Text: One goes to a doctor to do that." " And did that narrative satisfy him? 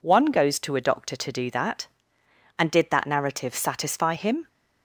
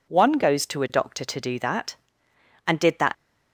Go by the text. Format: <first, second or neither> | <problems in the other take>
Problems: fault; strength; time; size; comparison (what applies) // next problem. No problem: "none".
first | stops before "narrative satisfy him"; at 3.1 s